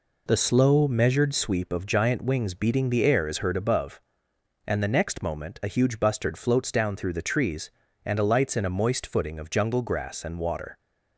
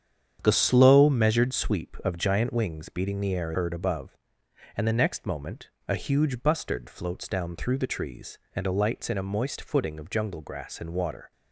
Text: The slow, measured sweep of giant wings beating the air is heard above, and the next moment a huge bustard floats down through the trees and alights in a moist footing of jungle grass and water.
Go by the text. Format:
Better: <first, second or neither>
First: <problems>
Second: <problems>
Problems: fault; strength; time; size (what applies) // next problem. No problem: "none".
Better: first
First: none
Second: starts louder than the rest; strong; until 1.4 s; 8.5 dB // skips "is"; at 3.5 s // pauses between "moment" and "a"; slight; at 5.6 s; 0.18 s long